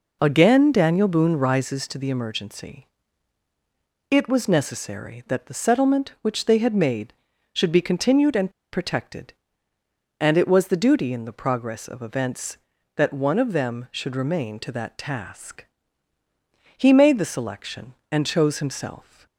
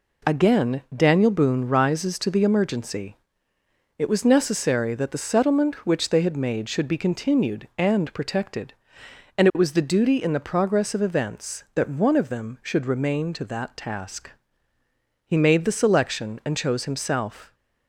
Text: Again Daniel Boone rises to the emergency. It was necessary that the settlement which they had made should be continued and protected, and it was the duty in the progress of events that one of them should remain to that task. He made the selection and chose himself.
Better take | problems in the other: second | pauses between "and" and "protected"; slight; at 8.5 s; 0.21 s long

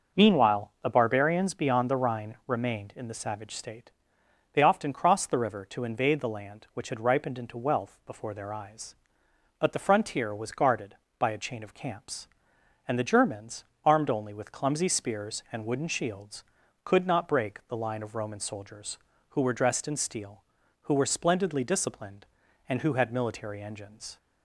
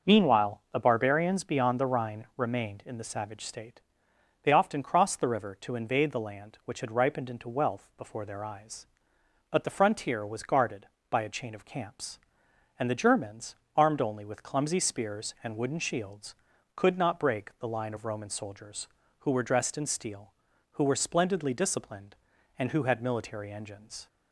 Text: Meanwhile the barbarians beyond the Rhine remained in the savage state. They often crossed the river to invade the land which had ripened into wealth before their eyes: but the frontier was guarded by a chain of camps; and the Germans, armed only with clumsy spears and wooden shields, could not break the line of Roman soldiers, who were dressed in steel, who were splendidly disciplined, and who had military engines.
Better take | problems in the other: neither | none

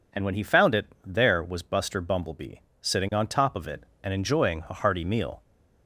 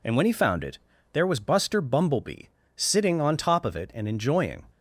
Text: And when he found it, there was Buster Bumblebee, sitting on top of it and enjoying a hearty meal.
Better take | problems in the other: first | stops before "a hearty meal"; at 4.6 s

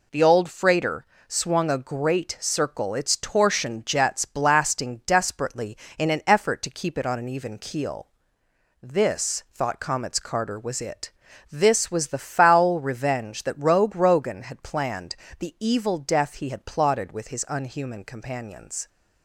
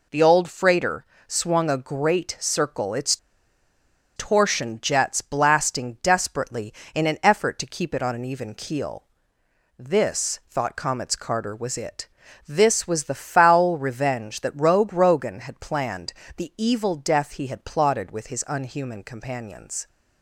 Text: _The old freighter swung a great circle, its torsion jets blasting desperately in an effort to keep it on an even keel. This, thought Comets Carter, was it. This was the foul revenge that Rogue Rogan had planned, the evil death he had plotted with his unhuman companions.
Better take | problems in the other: first | pauses between "freighter" and "swung"; slight; at 1.0 s; 0.22 s long; slight in the first // pauses between "its" and "torsion"; at 3.1 s; 0.99 s long

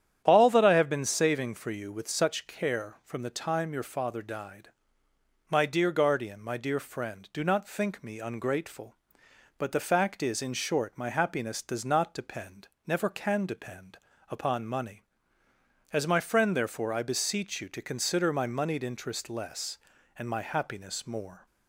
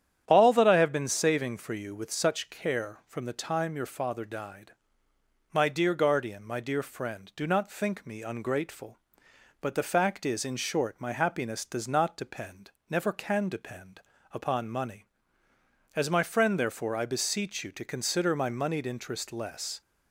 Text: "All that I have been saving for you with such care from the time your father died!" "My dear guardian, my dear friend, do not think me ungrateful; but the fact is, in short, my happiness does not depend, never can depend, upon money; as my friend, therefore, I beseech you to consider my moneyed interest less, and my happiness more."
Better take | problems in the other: first | starts louder than the rest; strong; until 1.2 s; 9.5 dB; strong in the first // stops before "and my happiness more"; at 19.8 s

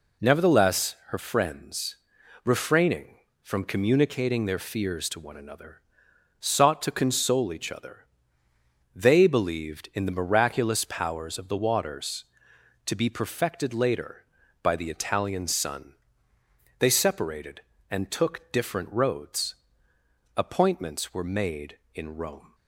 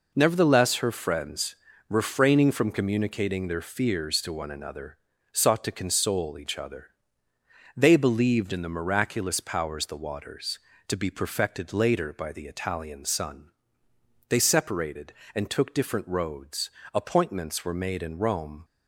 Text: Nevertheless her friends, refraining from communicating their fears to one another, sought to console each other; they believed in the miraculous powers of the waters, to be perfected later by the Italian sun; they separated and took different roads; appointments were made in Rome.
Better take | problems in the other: first | skips "of"; at 9.8 s

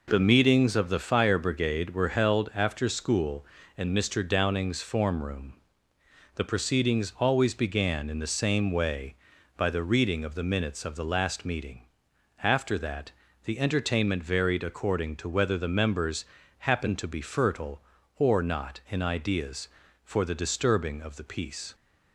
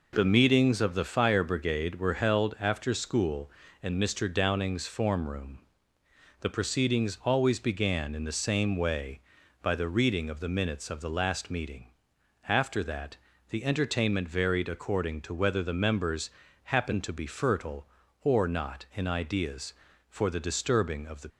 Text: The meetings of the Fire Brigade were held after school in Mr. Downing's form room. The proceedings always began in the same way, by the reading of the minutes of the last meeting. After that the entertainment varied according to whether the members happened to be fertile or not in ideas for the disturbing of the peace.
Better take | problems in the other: first | pauses between "that" and "the"; slight; at 13.1 s; 0.34 s long; slight in the first // pauses between "members" and "happened"; slight; at 16.2 s; 0.32 s long; slight in the first // stops before "peace"; at 21.2 s

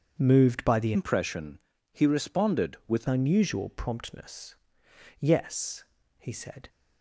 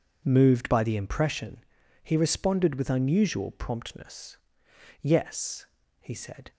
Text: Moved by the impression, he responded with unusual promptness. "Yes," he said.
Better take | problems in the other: second | starts louder than the rest; strong; until 1.2 s; 7.5 dB // changes voice from "impression" to "with"; from 0.9 to 3.0 s; 2.1 s long

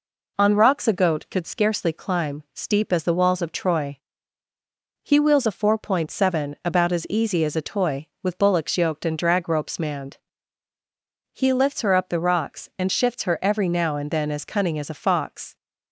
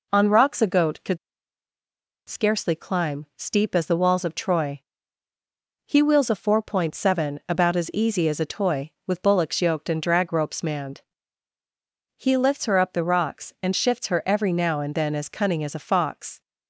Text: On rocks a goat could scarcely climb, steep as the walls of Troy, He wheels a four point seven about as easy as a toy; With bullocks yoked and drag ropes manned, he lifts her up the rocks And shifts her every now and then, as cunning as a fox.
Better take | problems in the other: first | pauses between "could" and "scarcely"; at 1.1 s; 1.1 s long

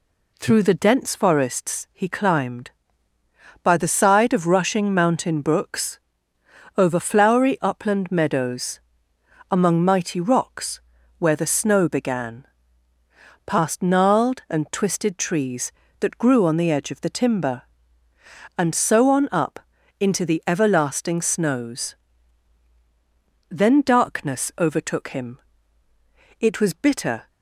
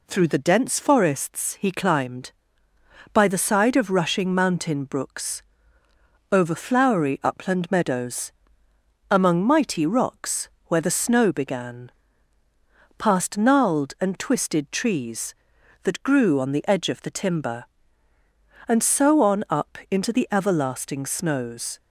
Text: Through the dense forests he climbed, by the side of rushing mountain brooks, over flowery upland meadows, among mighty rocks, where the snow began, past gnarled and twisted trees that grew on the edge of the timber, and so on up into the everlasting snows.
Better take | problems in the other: second | pauses between "up" and "into"; at 19.5 s; 0.38 s long // goes on to say "Then darkness overtook him It was bitter"; strong; from 23.4 s on; 3.7 s long

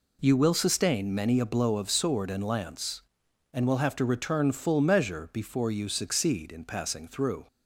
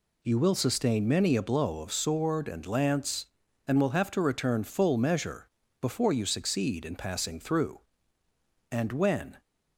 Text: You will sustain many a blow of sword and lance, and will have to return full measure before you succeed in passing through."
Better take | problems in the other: first | pauses between "measure" and "before"; slight; at 5.4 s; 0.32 s long // goes on to say "And when"; noticeable; from 8.6 s on; 0.72 s long

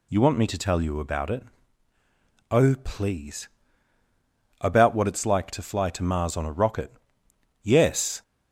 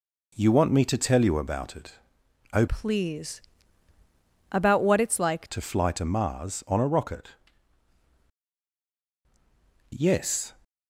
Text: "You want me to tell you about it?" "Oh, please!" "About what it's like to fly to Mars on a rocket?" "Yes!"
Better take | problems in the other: first | changes voice from "please" to "like"; from 2.6 to 5.4 s; 2.8 s long

